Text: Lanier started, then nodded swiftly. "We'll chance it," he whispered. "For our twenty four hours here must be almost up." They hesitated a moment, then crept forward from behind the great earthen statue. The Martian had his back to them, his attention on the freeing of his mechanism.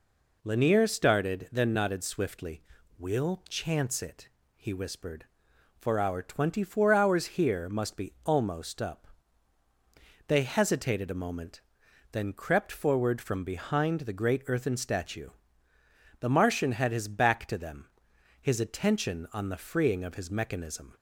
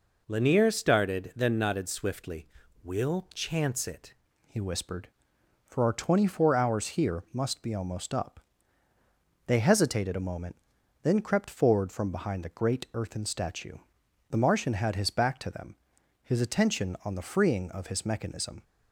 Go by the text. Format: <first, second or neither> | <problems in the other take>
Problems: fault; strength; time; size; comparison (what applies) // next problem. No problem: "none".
first | changes voice at "he"; from 4.4 s on; 14.2 s long